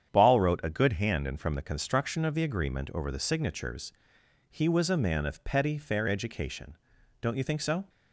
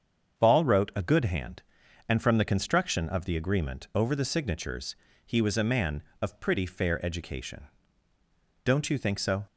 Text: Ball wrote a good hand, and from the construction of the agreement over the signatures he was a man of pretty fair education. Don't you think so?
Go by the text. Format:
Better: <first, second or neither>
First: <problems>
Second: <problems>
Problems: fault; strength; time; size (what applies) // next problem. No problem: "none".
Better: second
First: starts louder than the rest; strong; until 1.1 s; 8.5 dB // pauses between "signatures" and "he"; noticeable; at 3.9 s; 0.58 s long // says "petty" for "pretty"; at 5.4 s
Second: starts louder than the rest; until 1.4 s; 7 dB // pauses between "signatures" and "he"; slight; at 4.9 s; 0.30 s long